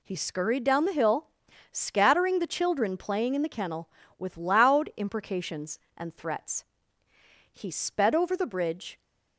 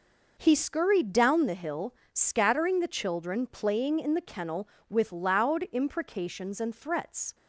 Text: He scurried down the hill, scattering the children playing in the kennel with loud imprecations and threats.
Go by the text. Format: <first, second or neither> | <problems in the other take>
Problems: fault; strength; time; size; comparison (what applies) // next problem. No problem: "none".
second | goes on to say "He sped over the bridge"; from 7.5 s on; 1.4 s long